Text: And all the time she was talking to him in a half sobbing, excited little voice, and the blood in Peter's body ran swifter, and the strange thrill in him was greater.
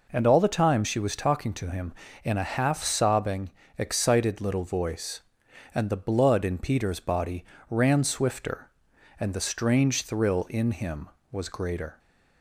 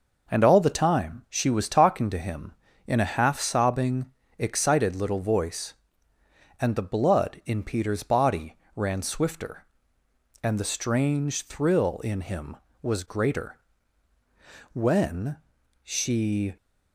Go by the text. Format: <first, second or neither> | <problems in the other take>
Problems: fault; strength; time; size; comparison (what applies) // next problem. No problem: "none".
first | pauses between "body" and "ran"; slight; at 8.5 s; 0.20 s long; slight in the first // goes on to say "When she"; strong; from 14.7 s on; 1.8 s long